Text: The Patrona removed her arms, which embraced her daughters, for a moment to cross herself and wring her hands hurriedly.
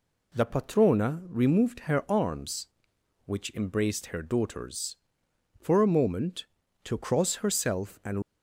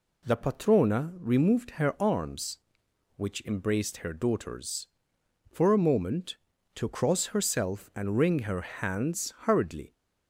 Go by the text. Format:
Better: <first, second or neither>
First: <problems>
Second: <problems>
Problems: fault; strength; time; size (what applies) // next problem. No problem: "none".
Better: second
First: stops before "wring her hands hurriedly"; at 8.2 s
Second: none